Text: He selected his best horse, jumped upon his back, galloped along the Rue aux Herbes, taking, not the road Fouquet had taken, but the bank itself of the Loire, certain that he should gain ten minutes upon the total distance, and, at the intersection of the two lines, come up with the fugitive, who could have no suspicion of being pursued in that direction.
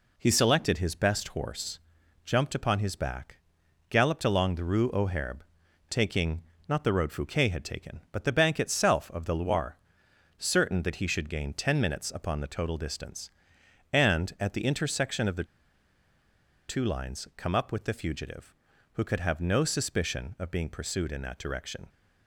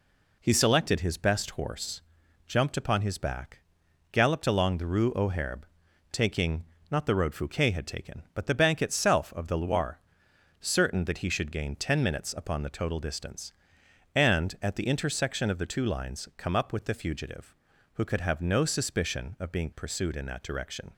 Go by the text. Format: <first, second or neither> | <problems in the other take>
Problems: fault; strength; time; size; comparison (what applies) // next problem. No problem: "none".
second | pauses between "the" and "two"; at 15.4 s; 1.2 s long